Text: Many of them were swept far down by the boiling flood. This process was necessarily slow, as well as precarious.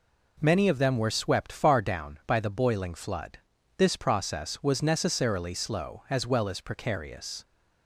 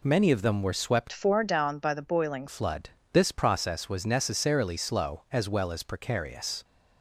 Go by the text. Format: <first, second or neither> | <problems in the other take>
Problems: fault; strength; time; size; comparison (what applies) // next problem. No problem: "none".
first | changes voice from "far" to "boiling"; from 1.1 to 2.4 s; 1.3 s long